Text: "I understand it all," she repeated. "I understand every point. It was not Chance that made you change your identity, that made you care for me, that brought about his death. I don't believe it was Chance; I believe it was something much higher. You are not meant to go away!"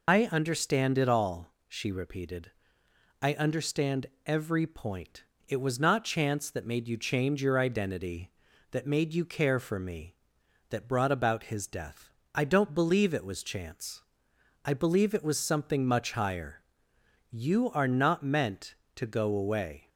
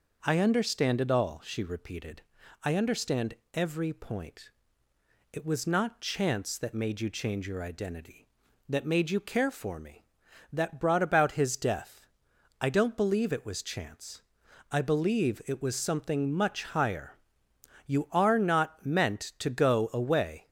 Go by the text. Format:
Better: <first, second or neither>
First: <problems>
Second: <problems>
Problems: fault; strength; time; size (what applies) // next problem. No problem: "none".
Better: second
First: loses the start of "I"; at 0.0 s; 90 ms // pauses between "understand" and "every"; slight; at 4.0 s; 0.20 s long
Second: pauses between "understand" and "every"; slight; at 3.3 s; 0.20 s long